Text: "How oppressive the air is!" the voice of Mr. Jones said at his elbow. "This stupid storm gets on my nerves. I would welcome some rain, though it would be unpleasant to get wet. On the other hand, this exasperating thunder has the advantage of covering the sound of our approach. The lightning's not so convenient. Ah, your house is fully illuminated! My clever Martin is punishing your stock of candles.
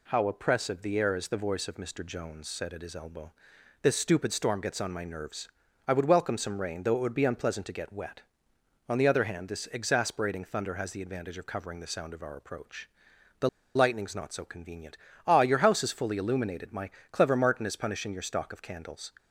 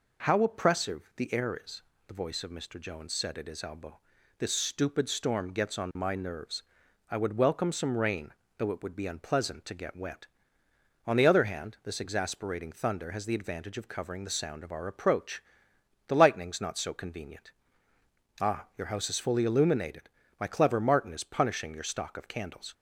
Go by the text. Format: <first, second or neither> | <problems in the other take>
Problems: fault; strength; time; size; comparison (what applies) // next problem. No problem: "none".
second | pauses between "The" and "lightning's"; slight; at 13.4 s; 0.26 s long // pauses between "My" and "clever"; slight; at 16.8 s; 0.22 s long